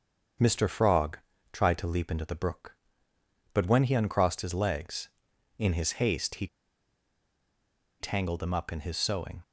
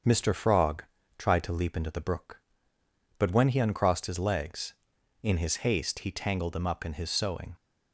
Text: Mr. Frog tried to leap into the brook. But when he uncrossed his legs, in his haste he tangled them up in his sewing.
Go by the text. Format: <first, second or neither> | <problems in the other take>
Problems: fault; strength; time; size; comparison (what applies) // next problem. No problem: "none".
second | starts louder than the rest; until 1.7 s; 7 dB; also in the second // pauses between "Frog" and "tried"; slight; at 1.1 s; 0.32 s long; slight in the second // pauses between "he" and "tangled"; strong; at 6.4 s; 1.5 s long